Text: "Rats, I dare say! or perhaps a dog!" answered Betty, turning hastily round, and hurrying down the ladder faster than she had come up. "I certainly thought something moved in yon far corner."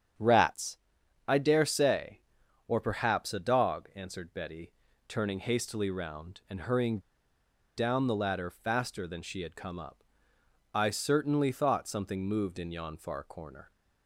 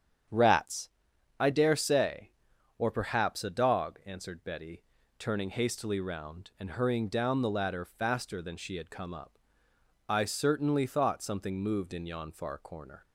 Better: second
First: starts louder than the rest; strong; until 1.6 s; 8.5 dB // pauses between "hurrying" and "down"; noticeable; at 6.9 s; 0.76 s long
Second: starts louder than the rest; strong; until 1.8 s; 8 dB

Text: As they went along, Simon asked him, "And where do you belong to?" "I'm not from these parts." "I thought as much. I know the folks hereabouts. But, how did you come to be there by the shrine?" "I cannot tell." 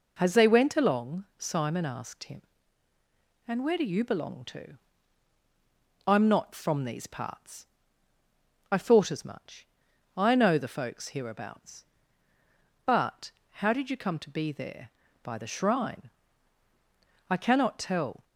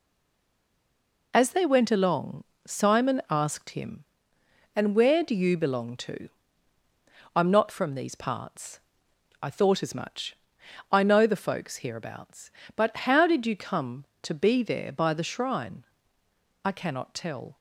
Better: first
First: none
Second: stays silent before the first word; noticeable; until 1.3 s; 1.3 s long

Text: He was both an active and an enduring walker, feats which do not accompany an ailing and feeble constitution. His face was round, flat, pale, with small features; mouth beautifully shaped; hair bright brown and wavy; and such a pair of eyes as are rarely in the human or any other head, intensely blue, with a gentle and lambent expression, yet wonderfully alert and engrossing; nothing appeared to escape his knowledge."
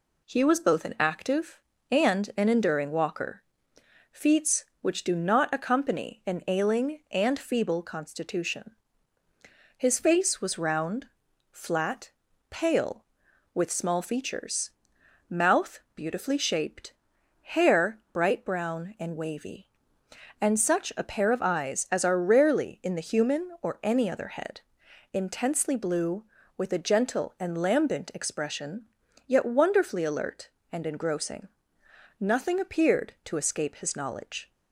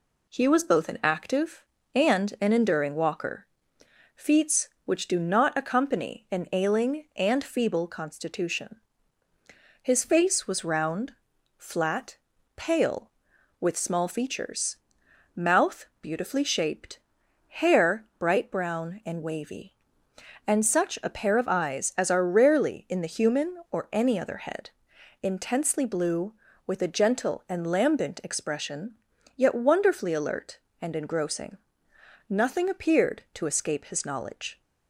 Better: neither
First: pauses between "mouth" and "beautifully"; slight; at 15.7 s; 0.16 s long // pauses between "hair" and "bright"; slight; at 17.9 s; 0.16 s long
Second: pauses between "mouth" and "beautifully"; slight; at 15.8 s; 0.16 s long // pauses between "hair" and "bright"; slight; at 18.0 s; 0.16 s long

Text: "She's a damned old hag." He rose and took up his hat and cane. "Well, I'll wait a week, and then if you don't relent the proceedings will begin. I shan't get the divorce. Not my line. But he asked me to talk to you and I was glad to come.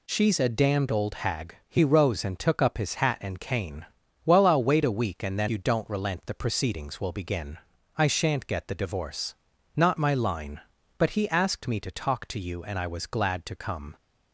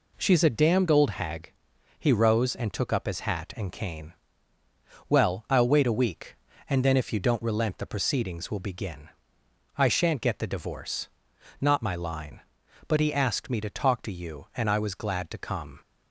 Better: second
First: skips "if"; at 5.4 s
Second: none

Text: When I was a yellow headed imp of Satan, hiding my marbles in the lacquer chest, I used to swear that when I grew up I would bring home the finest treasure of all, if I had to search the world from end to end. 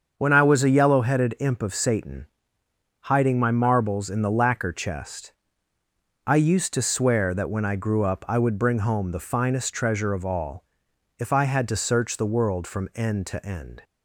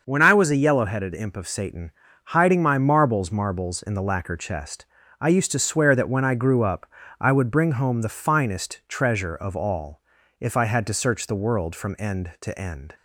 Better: first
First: starts louder than the rest; until 1.1 s; 7 dB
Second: starts louder than the rest; until 1.0 s; 6 dB // says "marbles" twice; at 3.3 s // pauses between "up" and "I"; slight; at 6.8 s; 0.34 s long

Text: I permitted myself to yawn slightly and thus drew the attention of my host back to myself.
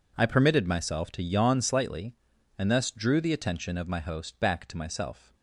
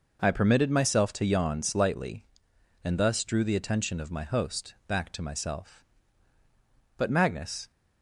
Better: first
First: none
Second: goes on to say "But Magnus"; noticeable; from 6.9 s on; 0.72 s long

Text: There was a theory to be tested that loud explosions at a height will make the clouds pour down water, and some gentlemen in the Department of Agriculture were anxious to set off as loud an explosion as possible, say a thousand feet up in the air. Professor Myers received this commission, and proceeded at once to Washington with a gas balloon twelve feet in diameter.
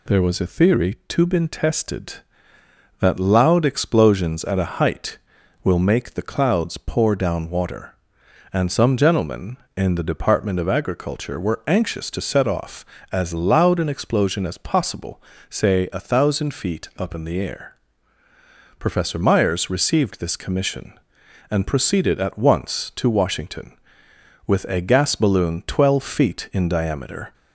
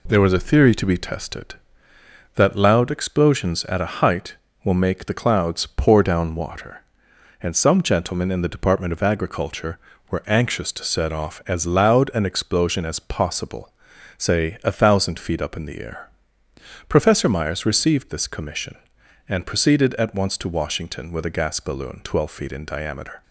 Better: second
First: says "been" for "be"; at 1.2 s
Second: none

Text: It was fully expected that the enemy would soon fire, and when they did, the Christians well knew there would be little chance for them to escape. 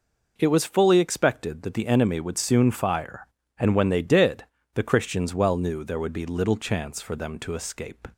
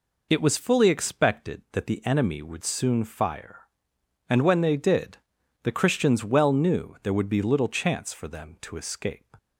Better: neither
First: none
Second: none

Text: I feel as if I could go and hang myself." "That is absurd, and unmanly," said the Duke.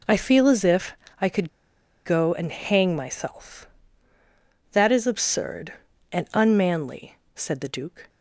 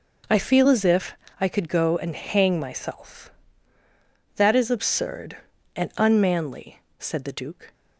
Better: second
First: pauses between "if" and "I"; slight; at 0.9 s; 0.28 s long // pauses between "could" and "go"; noticeable; at 1.4 s; 0.56 s long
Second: pauses between "if" and "I"; slight; at 1.1 s; 0.26 s long

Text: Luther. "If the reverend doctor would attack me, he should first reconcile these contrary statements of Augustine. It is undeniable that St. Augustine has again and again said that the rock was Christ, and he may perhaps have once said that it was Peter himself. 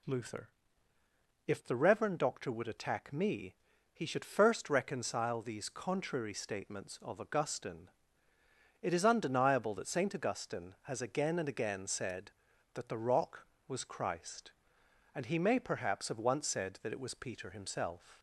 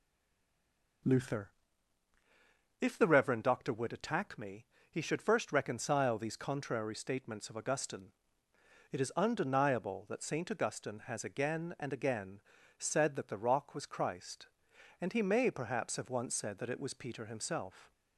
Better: first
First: none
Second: stays silent before the first word; until 1.0 s; 1.0 s long // pauses between "again" and "said"; at 12.4 s; 0.38 s long

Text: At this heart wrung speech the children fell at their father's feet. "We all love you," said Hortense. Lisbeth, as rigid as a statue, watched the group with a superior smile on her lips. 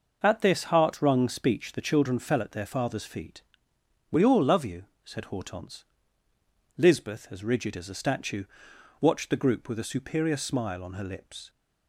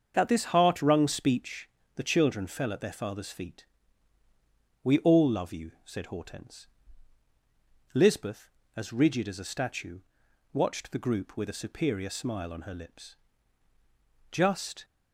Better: first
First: none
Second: starts louder than the rest; until 1.1 s; 7 dB // pauses between "speech" and "the"; slight; at 1.6 s; 0.28 s long // goes on to say "Just"; from 14.3 s on; 0.54 s long

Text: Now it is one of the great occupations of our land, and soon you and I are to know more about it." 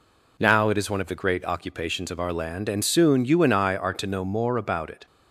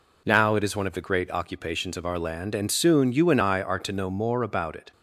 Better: neither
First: none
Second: none

